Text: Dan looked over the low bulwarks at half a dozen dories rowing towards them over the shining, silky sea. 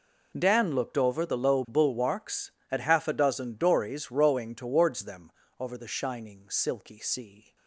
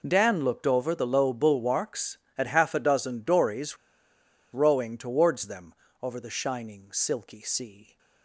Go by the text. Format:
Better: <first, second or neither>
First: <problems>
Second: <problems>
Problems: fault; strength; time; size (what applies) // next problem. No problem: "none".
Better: first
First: pauses between "them" and "over"; slight; at 5.3 s; 0.28 s long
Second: pauses between "dories" and "rowing"; noticeable; at 3.7 s; 0.77 s long // pauses between "them" and "over"; slight; at 5.7 s; 0.28 s long